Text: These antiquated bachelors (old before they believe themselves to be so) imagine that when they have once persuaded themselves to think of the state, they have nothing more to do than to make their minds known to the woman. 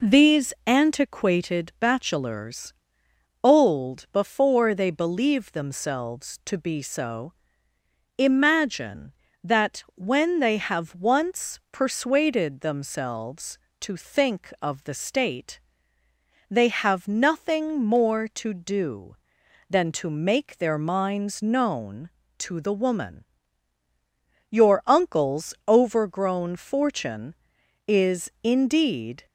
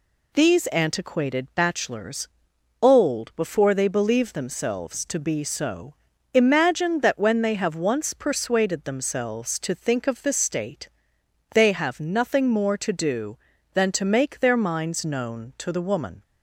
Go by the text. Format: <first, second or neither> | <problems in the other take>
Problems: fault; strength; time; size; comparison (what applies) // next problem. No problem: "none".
second | goes on to say "Your uncle's overgrown fortune is indeed"; strong; from 24.4 s on; 4.7 s long